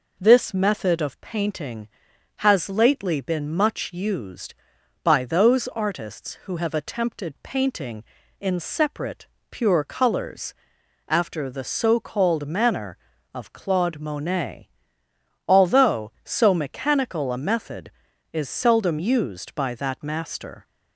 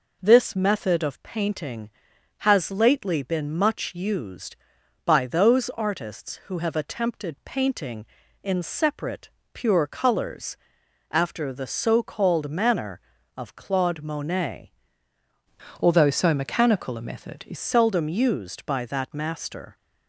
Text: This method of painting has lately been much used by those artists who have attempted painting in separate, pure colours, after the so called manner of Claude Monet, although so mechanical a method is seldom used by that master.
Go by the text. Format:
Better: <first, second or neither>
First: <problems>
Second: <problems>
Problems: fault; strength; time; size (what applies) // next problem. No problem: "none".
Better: first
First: none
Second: changes voice from "although" to "is"; from 15.8 to 17.5 s; 1.7 s long